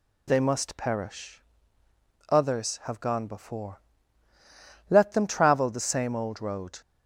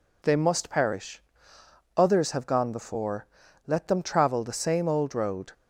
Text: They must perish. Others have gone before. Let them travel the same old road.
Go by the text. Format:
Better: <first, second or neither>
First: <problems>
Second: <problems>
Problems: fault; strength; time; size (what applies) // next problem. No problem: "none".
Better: neither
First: none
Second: none